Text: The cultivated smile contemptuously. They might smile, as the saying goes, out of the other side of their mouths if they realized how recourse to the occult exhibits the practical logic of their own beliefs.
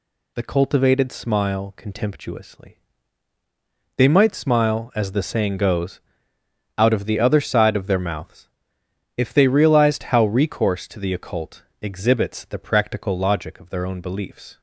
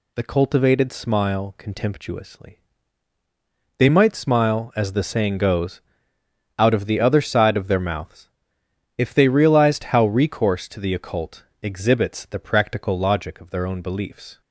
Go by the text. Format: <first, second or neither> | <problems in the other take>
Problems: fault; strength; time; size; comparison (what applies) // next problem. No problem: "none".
neither | pauses between "mouths" and "if"; noticeable; the same in both // pauses between "occult" and "exhibits"; slight; the same in both